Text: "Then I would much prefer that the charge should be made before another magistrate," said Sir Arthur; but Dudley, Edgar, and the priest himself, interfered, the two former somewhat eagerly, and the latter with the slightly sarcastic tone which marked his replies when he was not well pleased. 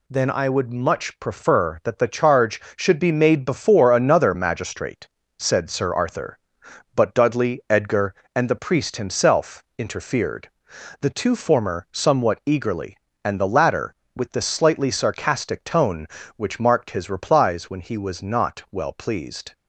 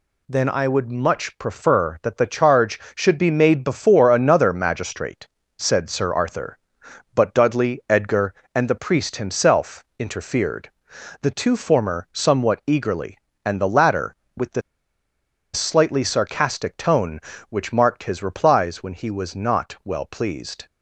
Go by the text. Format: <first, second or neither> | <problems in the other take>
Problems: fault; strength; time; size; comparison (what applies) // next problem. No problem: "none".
first | pauses between "the" and "slightly"; noticeable; at 14.6 s; 0.94 s long